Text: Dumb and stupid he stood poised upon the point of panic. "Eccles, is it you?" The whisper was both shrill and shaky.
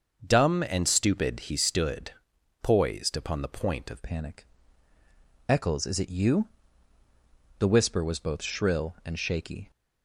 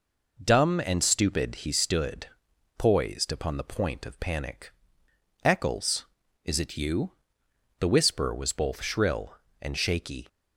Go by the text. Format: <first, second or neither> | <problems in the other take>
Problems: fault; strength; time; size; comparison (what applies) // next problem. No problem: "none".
second | starts louder than the rest; until 1.2 s; 6.5 dB // pauses between "stood" and "poised"; noticeable; at 2.1 s; 0.48 s long; noticeable in the second // changes voice at "panic"; from 4.0 s on; 5.7 s long